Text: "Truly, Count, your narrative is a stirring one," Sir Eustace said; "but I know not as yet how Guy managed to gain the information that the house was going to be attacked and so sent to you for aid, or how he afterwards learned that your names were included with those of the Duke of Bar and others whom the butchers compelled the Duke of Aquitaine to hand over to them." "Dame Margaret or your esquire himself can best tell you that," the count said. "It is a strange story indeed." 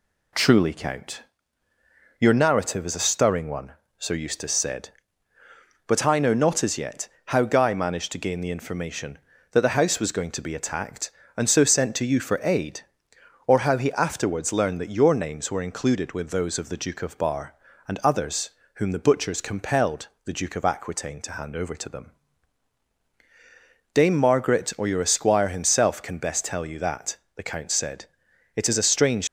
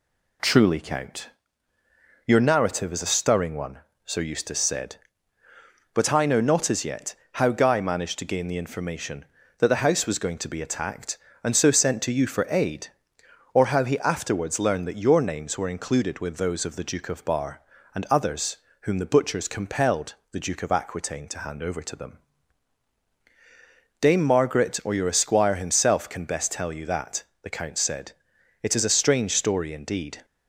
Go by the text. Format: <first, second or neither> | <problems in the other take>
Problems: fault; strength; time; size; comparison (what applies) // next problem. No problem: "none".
second | pauses between "yet" and "how"; slight; at 7.0 s; 0.18 s long; slight in the second // pauses between "others" and "whom"; slight; at 18.4 s; 0.24 s long; slight in the second // pauses between "compelled" and "the"; slight; at 20.0 s; 0.18 s long; slight in the second // stops before "story indeed"; at 29.2 s